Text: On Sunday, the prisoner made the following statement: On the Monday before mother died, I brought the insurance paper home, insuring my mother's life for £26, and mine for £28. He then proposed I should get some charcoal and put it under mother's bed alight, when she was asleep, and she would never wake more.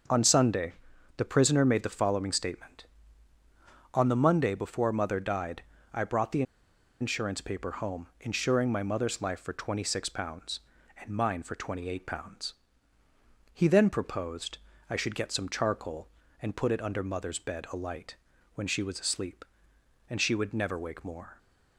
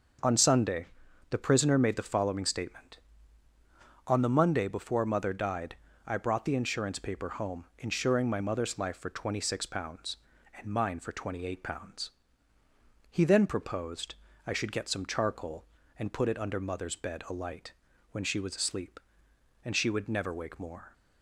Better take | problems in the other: second | starts louder than the rest; until 1.5 s; 6.5 dB; also in the second // pauses between "the" and "insurance"; noticeable; at 6.4 s; 0.58 s long // pauses between "proposed" and "I"; slight; at 14.5 s; 0.30 s long; slight in the second

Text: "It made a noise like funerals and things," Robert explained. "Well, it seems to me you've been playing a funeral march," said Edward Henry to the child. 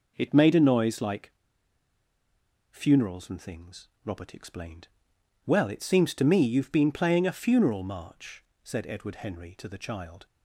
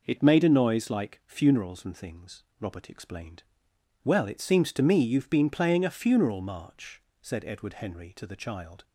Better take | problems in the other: second | pauses between "like" and "funerals"; strong; at 1.3 s; 1.3 s long

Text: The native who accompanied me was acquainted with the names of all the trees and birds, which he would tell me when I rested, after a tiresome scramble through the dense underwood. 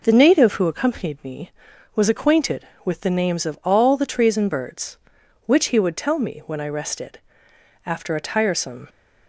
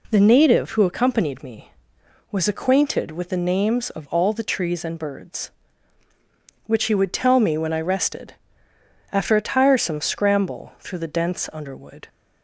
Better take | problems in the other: second | stops before "scramble through the dense underwood"; at 8.8 s

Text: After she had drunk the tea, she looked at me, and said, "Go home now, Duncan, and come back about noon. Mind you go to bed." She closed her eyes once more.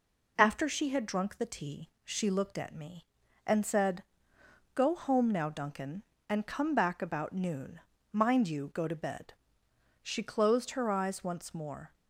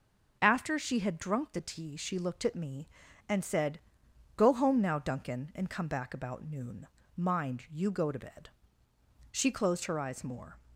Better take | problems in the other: first | skips "once"; at 10.2 s

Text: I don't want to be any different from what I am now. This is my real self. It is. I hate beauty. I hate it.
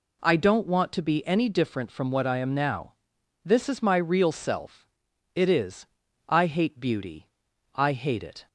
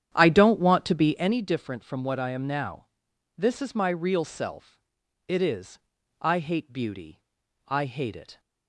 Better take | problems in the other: first | starts louder than the rest; strong; until 1.4 s; 9.5 dB

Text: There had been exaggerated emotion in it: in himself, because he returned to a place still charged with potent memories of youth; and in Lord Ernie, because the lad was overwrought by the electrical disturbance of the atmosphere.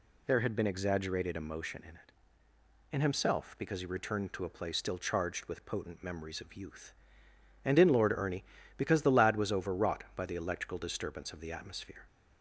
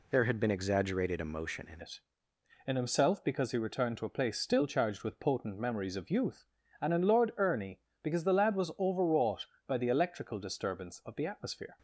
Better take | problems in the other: first | changes voice at "it"; from 1.8 s on; 9.9 s long

